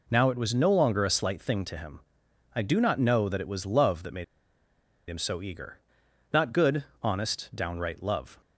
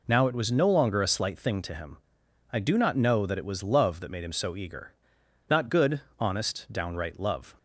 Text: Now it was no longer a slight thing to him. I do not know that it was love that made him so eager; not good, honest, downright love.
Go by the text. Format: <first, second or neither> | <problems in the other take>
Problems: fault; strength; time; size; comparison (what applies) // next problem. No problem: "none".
second | pauses between "made" and "him"; noticeable; at 4.2 s; 0.83 s long